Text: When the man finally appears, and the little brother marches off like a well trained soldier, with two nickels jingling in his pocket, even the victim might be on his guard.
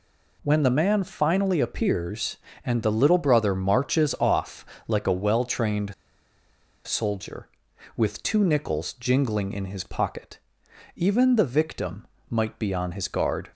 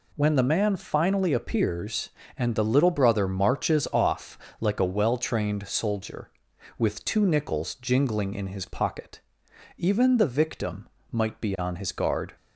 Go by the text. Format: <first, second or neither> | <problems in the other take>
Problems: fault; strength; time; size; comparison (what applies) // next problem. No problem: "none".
second | pauses between "off" and "like"; slight; at 4.6 s; 0.22 s long; slight in the second // pauses between "trained" and "soldier"; noticeable; at 5.9 s; 0.91 s long // pauses between "victim" and "might"; slight; at 12.0 s; 0.24 s long; slight in the second